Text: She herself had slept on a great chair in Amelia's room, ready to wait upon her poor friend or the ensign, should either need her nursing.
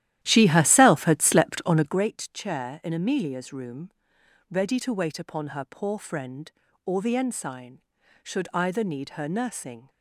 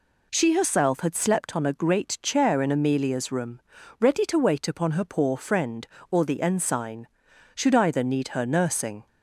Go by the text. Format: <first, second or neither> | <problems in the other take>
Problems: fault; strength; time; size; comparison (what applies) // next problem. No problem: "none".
second | starts louder than the rest; strong; until 2.1 s; 13 dB